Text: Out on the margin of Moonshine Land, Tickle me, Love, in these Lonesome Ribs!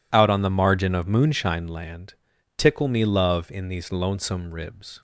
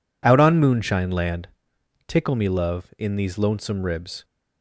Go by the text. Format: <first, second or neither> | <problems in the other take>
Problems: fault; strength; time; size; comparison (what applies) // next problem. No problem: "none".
first | skips "the margin of"; at 0.5 s